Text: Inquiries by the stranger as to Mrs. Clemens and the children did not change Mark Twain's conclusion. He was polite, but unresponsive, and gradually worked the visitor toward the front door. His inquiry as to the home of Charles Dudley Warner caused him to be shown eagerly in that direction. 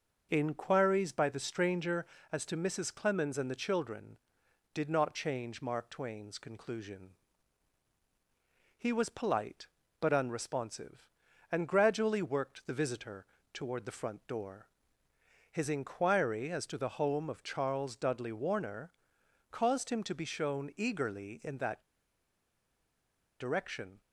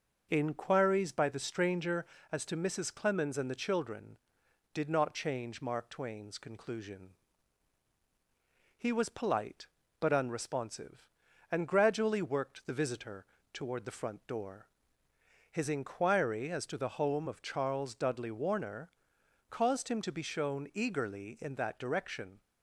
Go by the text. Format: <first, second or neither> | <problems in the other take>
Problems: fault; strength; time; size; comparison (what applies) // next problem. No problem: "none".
second | pauses between "visitor" and "toward"; slight; at 13.2 s; 0.30 s long; slight in the second // pauses between "Warner" and "caused"; noticeable; at 18.9 s; 0.58 s long; noticeable in the second // pauses between "that" and "direction"; strong; at 21.8 s; 1.5 s long